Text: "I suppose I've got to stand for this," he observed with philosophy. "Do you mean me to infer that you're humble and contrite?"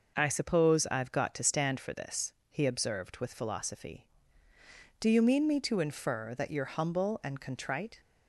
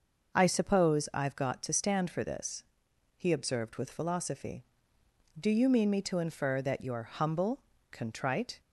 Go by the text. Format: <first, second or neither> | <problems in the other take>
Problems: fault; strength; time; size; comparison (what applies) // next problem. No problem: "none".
first | skips "and"; at 7.7 s